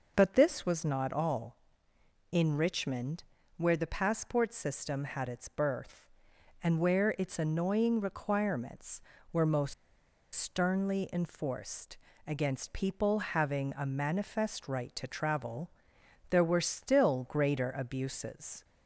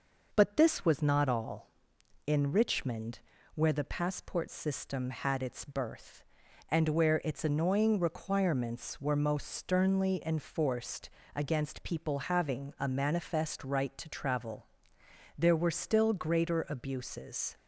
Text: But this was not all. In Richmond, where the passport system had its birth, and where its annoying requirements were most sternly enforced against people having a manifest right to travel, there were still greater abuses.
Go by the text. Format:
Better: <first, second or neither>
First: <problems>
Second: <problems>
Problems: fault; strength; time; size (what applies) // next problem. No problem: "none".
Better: second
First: pauses between "most" and "sternly"; noticeable; at 9.7 s; 0.59 s long // pauses between "enforced" and "against"; slight; at 11.9 s; 0.30 s long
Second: pauses between "enforced" and "against"; slight; at 11.0 s; 0.26 s long